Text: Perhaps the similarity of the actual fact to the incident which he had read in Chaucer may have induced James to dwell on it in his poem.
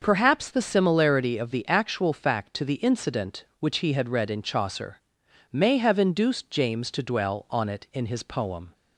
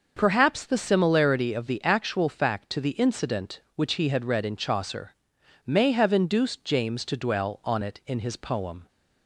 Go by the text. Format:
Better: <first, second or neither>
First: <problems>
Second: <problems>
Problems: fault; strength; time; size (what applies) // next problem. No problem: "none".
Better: neither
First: starts louder than the rest; until 1.0 s; 6 dB // pauses between "Chaucer" and "may"; noticeable; at 4.9 s; 0.54 s long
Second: starts louder than the rest; noticeable; until 1.1 s; 6 dB // pauses between "Chaucer" and "may"; noticeable; at 5.1 s; 0.54 s long